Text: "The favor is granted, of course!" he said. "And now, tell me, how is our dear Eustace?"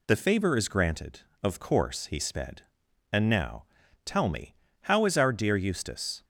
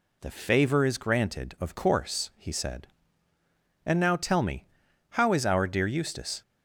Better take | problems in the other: second | says "sped" for "said"; at 2.1 s

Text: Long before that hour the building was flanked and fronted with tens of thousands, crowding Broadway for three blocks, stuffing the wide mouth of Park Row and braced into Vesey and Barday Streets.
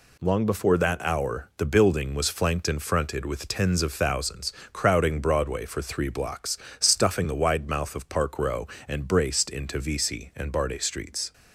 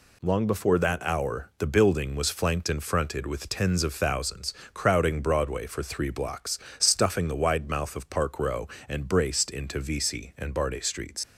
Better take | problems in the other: first | leaves "Streets" unfinished; at 11.2 s; 110 ms

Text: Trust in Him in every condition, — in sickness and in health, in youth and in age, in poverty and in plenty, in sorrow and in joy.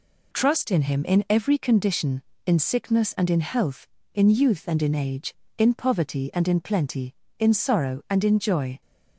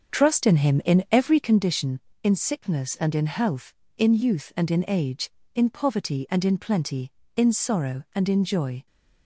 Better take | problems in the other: first | starts louder than the rest; until 1.7 s; 6.5 dB

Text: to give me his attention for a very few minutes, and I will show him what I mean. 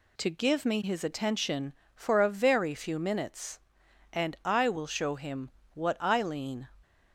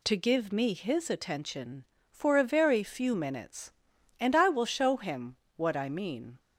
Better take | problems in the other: second | pauses between "him" and "what"; slight; at 5.5 s; 0.24 s long; slight in the second // says "lean" for "mean"; at 6.2 s

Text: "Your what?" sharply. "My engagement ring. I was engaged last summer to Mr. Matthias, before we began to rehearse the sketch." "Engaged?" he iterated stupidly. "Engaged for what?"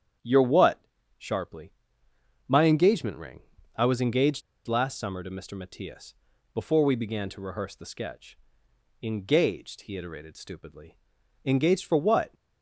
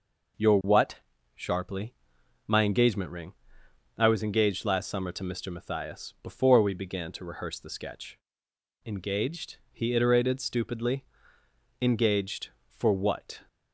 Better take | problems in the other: second | starts louder than the rest; strong; until 1.5 s; 9 dB // pauses between "engaged" and "last"; slight; at 4.4 s; 0.26 s long

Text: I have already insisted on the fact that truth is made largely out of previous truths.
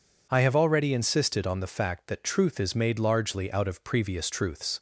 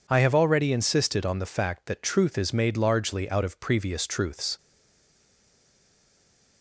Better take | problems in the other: first | stays silent after the last word; noticeable; from 4.5 s on; 2.1 s long

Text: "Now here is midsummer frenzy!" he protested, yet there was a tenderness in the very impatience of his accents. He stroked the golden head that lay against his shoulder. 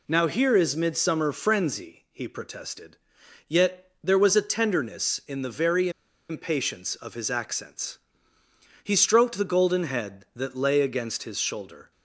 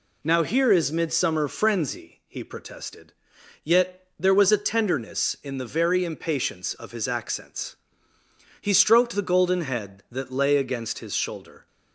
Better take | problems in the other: second | pauses between "very" and "impatience"; at 5.8 s; 0.40 s long

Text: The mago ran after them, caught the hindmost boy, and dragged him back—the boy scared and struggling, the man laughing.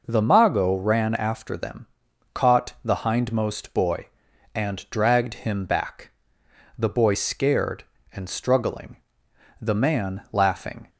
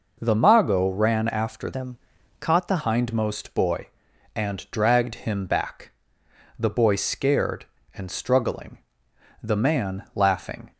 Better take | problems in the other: first | changes voice from "them" to "the"; from 1.7 to 2.8 s; 1.1 s long

